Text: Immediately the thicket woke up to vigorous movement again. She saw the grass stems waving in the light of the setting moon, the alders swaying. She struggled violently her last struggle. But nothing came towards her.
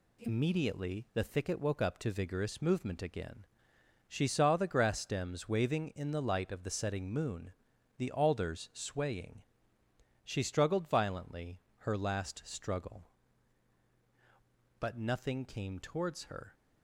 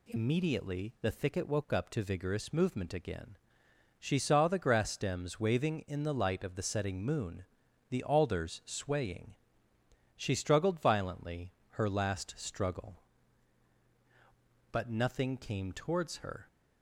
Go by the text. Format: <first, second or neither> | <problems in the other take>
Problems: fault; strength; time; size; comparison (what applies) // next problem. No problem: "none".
second | gets quieter; noticeable; throughout; 5 dB // pauses between "violently" and "her"; slight; at 11.6 s; 0.20 s long; slight in the second